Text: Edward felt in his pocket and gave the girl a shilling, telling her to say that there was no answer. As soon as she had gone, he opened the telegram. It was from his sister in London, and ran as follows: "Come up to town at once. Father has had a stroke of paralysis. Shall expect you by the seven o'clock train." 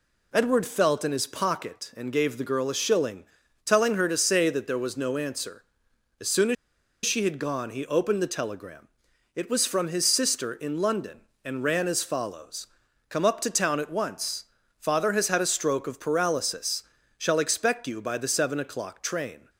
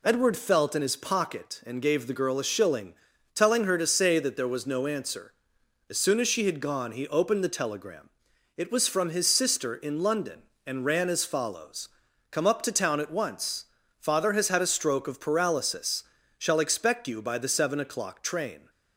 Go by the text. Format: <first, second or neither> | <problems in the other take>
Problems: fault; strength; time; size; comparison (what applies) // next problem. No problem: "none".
second | pauses between "as" and "she"; noticeable; at 6.5 s; 0.50 s long